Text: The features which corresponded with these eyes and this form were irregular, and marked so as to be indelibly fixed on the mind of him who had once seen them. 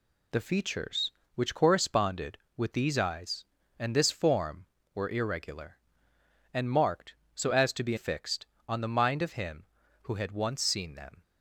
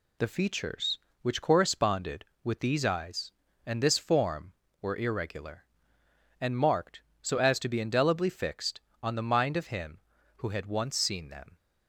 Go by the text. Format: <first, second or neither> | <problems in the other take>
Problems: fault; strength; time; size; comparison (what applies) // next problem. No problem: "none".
second | skips "indelibly"; at 7.9 s